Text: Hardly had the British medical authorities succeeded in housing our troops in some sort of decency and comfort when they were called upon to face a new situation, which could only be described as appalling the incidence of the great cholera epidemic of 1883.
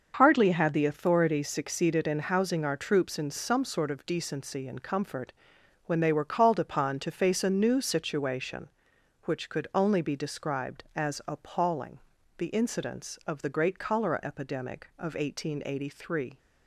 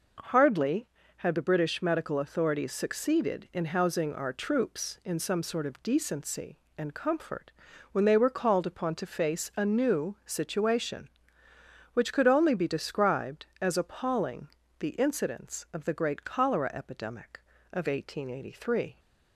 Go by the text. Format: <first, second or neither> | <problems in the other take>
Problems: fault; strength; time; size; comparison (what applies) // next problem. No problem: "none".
second | starts louder than the rest; until 1.1 s; 6.5 dB // skips "British medical"; at 0.8 s // pauses between "comfort" and "when"; noticeable; at 5.3 s; 0.54 s long; also in the second // pauses between "appalling" and "the"; at 11.9 s; 0.38 s long; slight in the second